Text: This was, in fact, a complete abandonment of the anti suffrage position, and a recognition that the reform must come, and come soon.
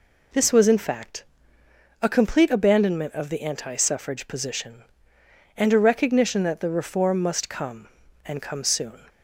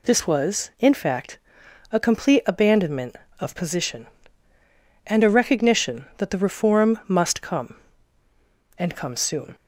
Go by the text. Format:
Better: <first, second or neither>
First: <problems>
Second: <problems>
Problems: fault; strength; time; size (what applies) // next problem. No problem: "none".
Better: first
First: none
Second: skips "the anti suffrage"; at 3.5 s